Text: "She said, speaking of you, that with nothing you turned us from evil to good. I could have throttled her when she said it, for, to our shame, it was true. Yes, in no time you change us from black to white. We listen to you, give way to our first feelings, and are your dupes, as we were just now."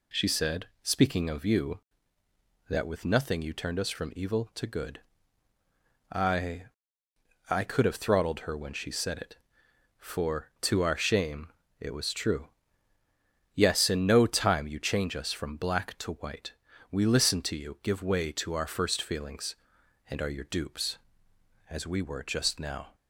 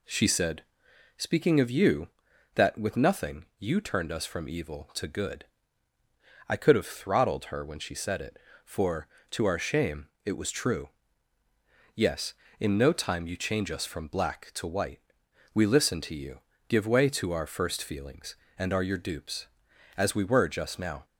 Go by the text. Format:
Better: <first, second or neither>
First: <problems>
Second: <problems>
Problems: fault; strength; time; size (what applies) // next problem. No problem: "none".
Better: second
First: says "I" twice; at 7.4 s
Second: none